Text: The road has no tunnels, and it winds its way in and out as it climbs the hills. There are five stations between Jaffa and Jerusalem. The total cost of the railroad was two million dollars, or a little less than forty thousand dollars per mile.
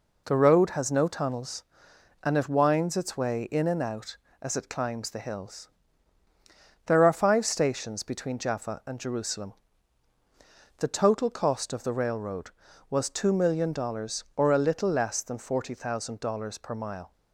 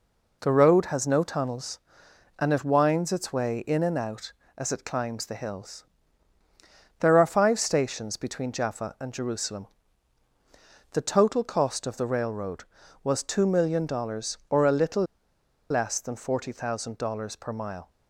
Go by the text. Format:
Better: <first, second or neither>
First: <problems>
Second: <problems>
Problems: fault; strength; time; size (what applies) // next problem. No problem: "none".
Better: first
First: none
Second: pauses between "little" and "less"; noticeable; at 15.0 s; 0.67 s long